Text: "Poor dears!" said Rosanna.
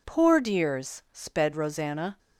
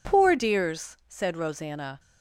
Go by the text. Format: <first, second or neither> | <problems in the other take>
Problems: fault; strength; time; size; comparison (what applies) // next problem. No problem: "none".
second | says "sped" for "said"; at 1.1 s